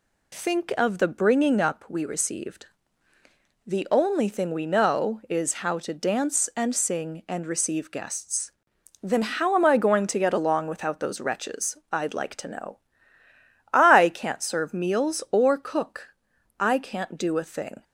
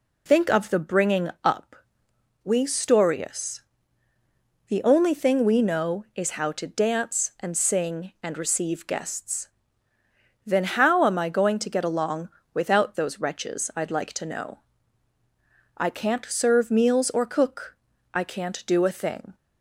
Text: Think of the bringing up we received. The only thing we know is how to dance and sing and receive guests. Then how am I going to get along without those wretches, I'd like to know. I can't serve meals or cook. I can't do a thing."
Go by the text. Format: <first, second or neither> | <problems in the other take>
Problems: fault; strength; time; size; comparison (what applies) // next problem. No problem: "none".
first | pauses between "up" and "we"; noticeable; at 1.7 s; 0.70 s long // says "storius" for "received"; at 2.6 s // pauses between "along" and "without"; slight; at 12.2 s; 0.26 s long